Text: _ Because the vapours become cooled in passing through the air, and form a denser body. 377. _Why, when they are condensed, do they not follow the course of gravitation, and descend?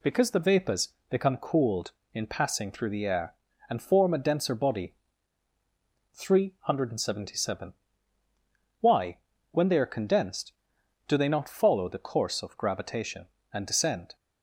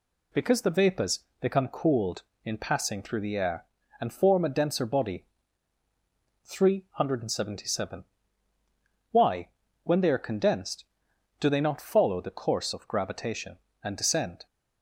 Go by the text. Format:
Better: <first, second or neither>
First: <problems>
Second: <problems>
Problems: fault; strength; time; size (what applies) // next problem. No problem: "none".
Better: neither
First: pauses between "vapours" and "become"; slight; at 0.8 s; 0.20 s long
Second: pauses between "vapours" and "become"; slight; at 1.1 s; 0.20 s long